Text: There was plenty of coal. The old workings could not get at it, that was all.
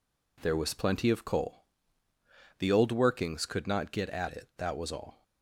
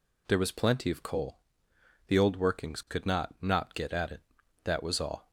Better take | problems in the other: first | says "not" twice; at 3.4 s

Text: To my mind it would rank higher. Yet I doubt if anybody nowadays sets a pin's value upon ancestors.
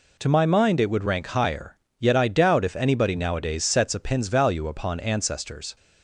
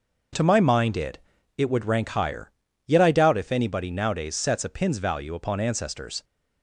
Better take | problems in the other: first | starts louder than the rest; until 1.7 s; 6.5 dB // says "it" twice; at 1.5 s

